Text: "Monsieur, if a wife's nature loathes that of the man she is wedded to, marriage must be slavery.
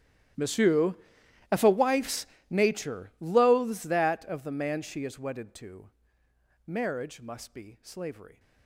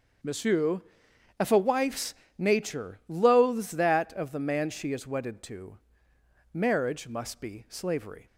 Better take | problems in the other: second | gets quieter; strong; throughout; 23.5 dB // starts louder than the rest; strong; until 1.9 s; 12.5 dB; also in the second // pauses between "wife's" and "nature"; slight; at 2.2 s; 0.24 s long; slight in the second

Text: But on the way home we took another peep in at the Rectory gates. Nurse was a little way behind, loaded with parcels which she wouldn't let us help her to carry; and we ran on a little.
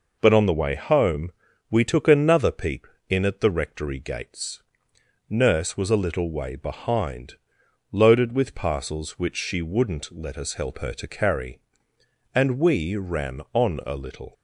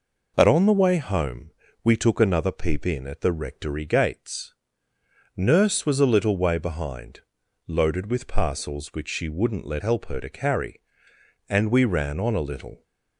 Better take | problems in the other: first | pauses between "home" and "we"; slight; at 1.5 s; 0.32 s long; also in the first // skips "us"; at 9.8 s

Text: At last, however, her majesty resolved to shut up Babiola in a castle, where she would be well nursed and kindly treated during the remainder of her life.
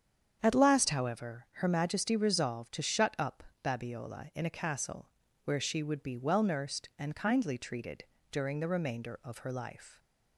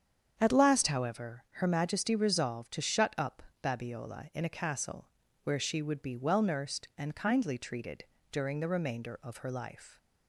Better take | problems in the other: neither | starts louder than the rest; strong; the same in both // pauses between "up" and "Babiola"; slight; the same in both // pauses between "treated" and "during"; slight; the same in both

